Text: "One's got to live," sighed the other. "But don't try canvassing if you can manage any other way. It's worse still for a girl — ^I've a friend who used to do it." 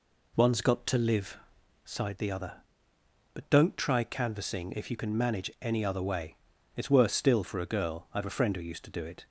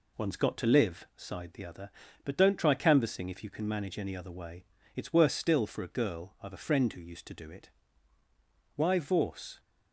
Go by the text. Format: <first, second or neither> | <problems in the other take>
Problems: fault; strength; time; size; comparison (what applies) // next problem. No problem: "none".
first | goes on to say "Why Vorse"; noticeable; from 8.7 s on; 0.84 s long